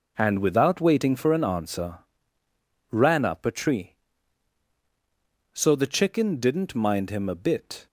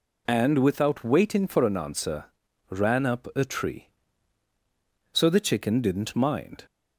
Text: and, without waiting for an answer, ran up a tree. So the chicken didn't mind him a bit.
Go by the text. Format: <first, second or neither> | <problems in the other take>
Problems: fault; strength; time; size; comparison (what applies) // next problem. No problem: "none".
first | stops before "him a bit"; at 6.6 s